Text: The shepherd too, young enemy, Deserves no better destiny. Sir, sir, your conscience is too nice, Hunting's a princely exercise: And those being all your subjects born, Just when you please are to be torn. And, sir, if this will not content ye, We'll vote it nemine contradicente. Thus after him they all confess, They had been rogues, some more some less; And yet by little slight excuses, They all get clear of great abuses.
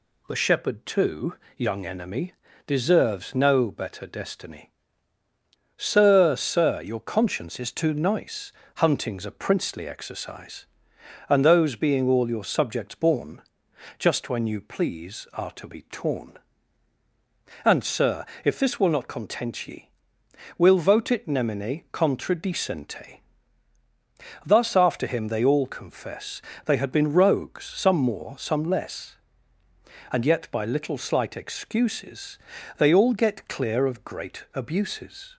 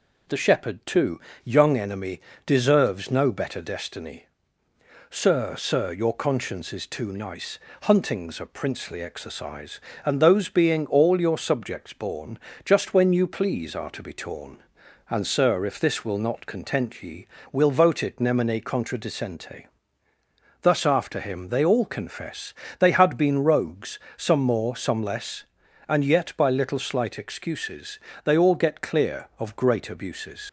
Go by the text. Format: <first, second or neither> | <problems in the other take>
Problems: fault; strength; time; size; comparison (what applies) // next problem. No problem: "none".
first | leaves "abuses" unfinished; at 30.4 s; 80 ms